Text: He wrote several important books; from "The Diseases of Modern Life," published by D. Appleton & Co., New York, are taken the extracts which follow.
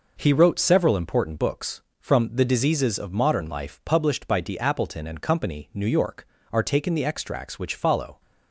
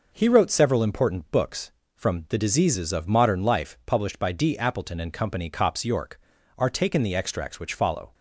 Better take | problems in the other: first | says "Cops" for "New"; at 5.4 s

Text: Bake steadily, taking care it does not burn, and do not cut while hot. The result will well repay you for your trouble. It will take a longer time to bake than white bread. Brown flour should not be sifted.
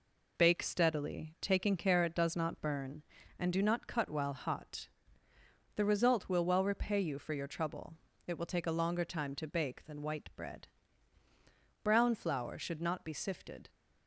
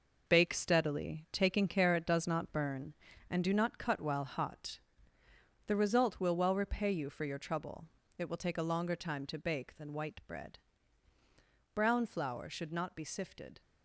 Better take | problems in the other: first | gets quieter; strong; throughout; 7.5 dB

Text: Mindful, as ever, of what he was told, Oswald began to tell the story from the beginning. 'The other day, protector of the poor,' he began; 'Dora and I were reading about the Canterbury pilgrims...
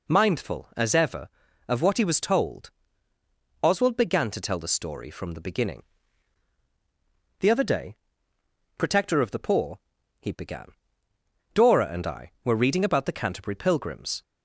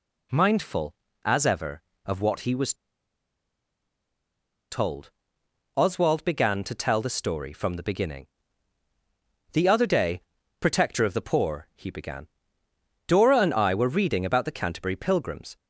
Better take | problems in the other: first | pauses between "was" and "told"; strong; at 2.7 s; 1.9 s long

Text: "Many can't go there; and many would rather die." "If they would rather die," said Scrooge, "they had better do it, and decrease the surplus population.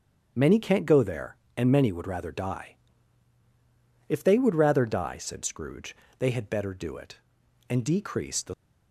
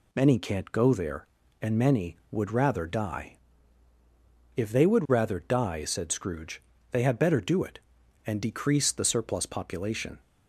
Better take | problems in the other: second | starts louder than the rest; strong; until 1.3 s; 7.5 dB // stops before "surplus population"; at 8.5 s

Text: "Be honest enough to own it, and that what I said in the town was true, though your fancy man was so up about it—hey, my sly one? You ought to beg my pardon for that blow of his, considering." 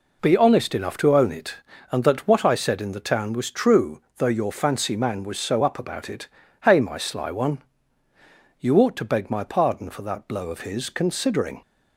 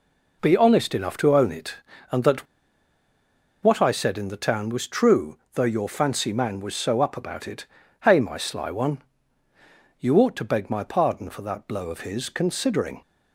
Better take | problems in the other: first | pauses between "that" and "what"; at 2.4 s; 1.1 s long

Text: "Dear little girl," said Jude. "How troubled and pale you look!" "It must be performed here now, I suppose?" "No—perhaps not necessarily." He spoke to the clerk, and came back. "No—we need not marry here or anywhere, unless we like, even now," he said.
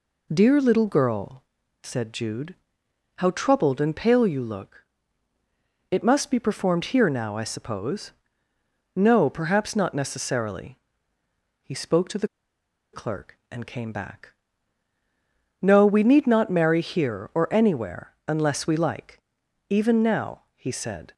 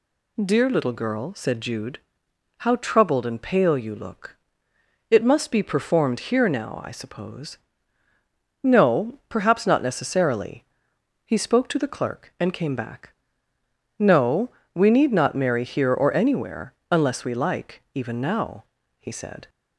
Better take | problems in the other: second | pauses between "the" and "clerk"; noticeable; at 12.2 s; 0.65 s long

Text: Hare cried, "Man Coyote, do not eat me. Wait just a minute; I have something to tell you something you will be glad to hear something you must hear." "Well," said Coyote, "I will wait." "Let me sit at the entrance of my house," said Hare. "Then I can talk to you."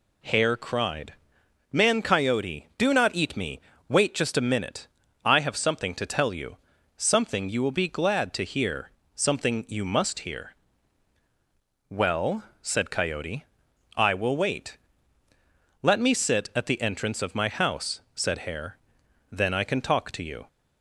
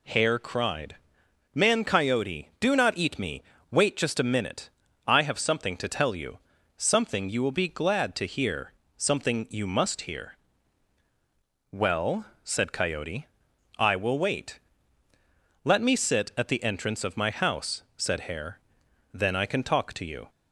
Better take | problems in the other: neither | pauses between "you" and "something"; the same in both // pauses between "hear" and "something"; slight; the same in both

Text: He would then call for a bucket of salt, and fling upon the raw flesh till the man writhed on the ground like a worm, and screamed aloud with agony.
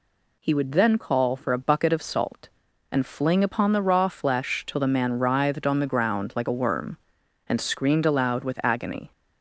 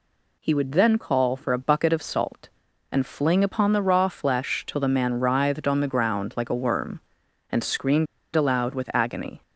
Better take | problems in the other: first | pauses between "screamed" and "aloud"; slight; at 8.0 s; 0.29 s long

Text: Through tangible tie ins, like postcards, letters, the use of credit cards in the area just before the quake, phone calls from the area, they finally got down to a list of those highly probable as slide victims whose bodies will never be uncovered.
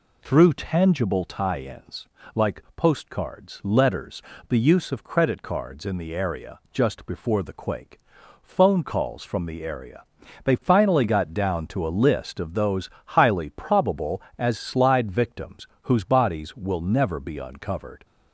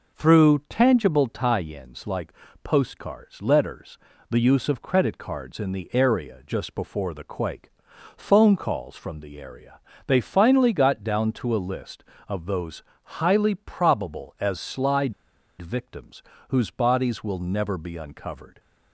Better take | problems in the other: first | pauses between "like" and "postcards"; slight; at 2.3 s; 0.30 s long // pauses between "those" and "highly"; slight; at 12.8 s; 0.22 s long; slight in the first // pauses between "slide" and "victims"; noticeable; at 15.1 s; 0.47 s long // pauses between "victims" and "whose"; slight; at 16.2 s; 0.28 s long; slight in the first

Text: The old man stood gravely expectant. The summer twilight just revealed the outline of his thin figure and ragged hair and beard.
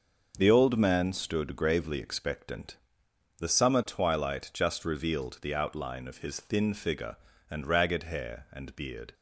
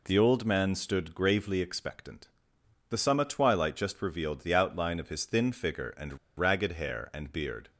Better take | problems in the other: first | pauses between "and" and "ragged"; slight; at 6.1 s; 0.20 s long

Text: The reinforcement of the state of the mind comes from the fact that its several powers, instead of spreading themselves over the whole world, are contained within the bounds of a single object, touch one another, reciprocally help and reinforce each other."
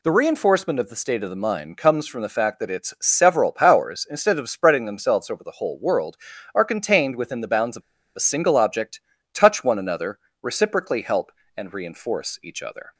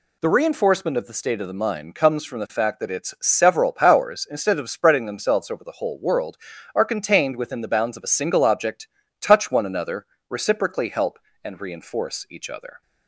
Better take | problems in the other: second | pauses between "of" and "a"; slight; at 7.8 s; 0.33 s long

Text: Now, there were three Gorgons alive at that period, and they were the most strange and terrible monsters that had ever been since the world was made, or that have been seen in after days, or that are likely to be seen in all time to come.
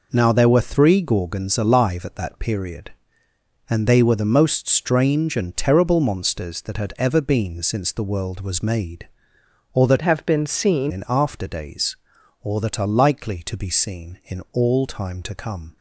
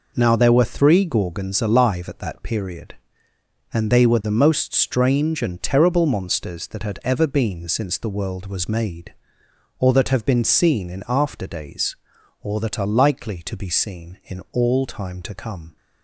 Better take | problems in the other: second | changes voice from "have" to "seen"; from 10.0 to 10.9 s; 0.9 s long

